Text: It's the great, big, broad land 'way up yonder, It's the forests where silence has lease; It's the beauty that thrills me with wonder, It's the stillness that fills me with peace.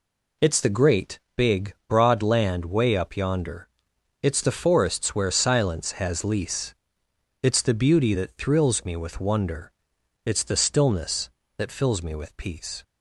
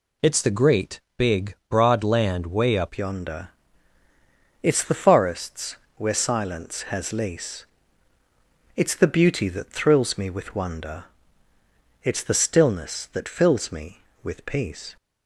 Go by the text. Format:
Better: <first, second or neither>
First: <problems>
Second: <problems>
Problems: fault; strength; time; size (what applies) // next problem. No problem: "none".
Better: first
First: none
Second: changes voice at "yonder"; from 2.9 s on; 12.0 s long // pauses between "forests" and "where"; slight; at 5.7 s; 0.20 s long